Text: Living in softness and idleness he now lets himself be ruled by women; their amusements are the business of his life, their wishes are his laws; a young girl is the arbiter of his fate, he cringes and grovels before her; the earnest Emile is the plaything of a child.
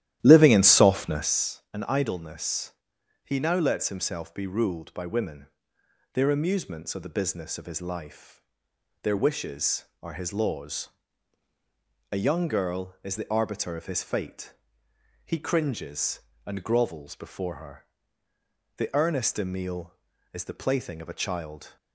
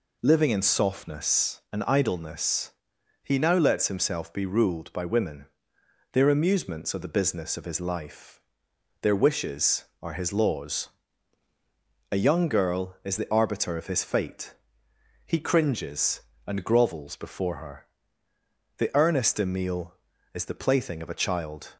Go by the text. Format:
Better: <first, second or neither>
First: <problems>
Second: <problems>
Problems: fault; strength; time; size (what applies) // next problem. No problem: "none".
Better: second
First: starts louder than the rest; strong; until 1.3 s; 13 dB // pauses between "idleness" and "he"; noticeable; at 2.7 s; 0.52 s long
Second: pauses between "idleness" and "he"; noticeable; at 2.7 s; 0.52 s long